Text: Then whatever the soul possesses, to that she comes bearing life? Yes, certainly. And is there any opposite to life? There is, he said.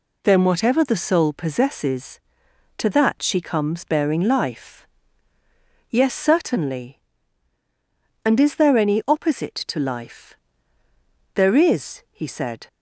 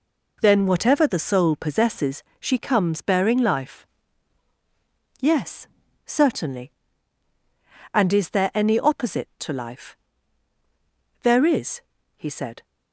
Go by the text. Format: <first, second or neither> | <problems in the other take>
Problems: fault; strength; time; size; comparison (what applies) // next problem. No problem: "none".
first | skips "to that"; at 2.3 s